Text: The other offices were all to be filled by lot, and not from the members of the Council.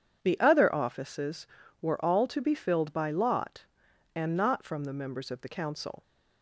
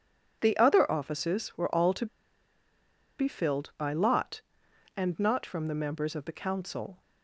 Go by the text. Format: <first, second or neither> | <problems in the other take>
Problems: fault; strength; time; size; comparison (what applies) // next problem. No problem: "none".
first | pauses between "to" and "be"; at 2.0 s; 1.1 s long